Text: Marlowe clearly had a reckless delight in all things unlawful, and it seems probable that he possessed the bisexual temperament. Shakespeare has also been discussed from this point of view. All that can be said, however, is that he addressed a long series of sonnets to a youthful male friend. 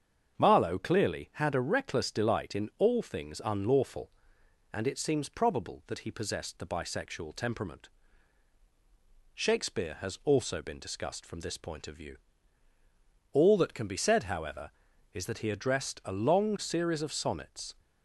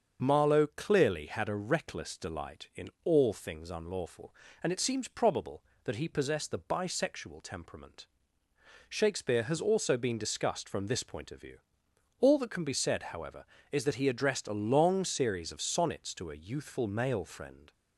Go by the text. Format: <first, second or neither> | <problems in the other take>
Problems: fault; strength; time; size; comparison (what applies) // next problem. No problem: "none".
second | starts louder than the rest; strong; until 1.4 s; 7 dB; also in the second // stops before "to a youthful male friend"; at 17.7 s